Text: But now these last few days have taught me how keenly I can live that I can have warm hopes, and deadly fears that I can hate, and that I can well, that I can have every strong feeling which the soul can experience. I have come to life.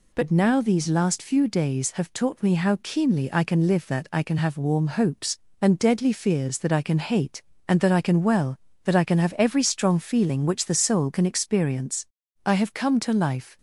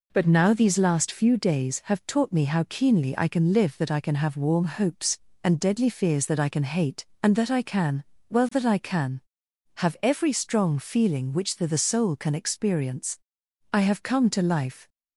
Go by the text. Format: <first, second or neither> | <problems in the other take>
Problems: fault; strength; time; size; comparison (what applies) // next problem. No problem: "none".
first | pauses between "can" and "well"; slight; at 8.0 s; 0.28 s long // says "the" twice; at 11.6 s